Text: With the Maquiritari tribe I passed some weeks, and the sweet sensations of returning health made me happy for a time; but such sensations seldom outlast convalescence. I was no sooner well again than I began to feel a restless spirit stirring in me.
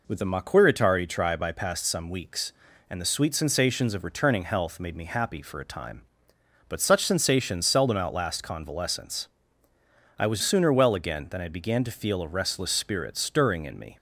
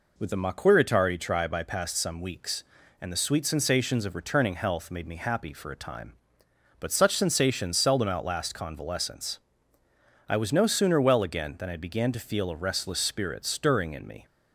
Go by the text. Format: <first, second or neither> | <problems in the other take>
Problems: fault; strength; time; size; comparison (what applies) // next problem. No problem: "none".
second | skips "no"; at 10.4 s